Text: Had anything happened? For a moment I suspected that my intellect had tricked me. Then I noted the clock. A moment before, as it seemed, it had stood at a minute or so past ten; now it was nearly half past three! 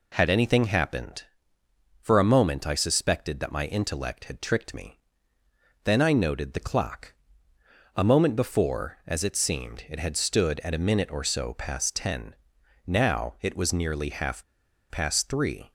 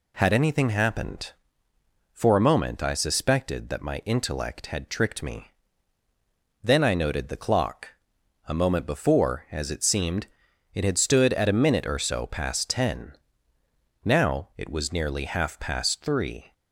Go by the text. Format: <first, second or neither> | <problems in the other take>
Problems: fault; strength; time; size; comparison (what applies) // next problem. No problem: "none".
second | pauses between "half" and "past"; noticeable; at 14.4 s; 0.48 s long